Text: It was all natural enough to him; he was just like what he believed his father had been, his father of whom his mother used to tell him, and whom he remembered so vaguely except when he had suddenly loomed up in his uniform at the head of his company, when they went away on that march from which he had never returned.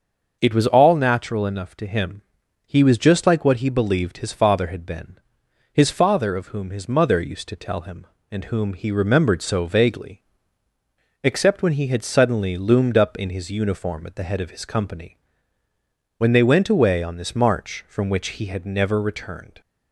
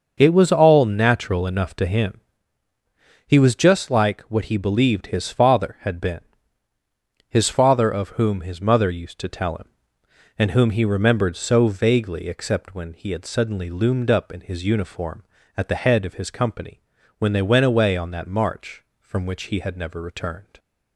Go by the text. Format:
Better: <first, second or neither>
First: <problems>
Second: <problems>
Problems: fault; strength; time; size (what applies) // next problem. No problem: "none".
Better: second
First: starts louder than the rest; until 1.4 s; 6.5 dB // pauses between "vaguely" and "except"; at 10.2 s; 1.0 s long // says "this" for "that"; at 17.1 s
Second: starts louder than the rest; until 1.1 s; 6.5 dB